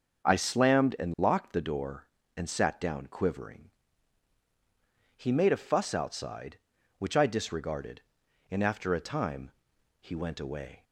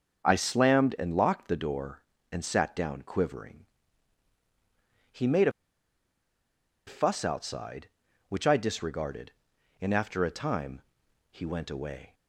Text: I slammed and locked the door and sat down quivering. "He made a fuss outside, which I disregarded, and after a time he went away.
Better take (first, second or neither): first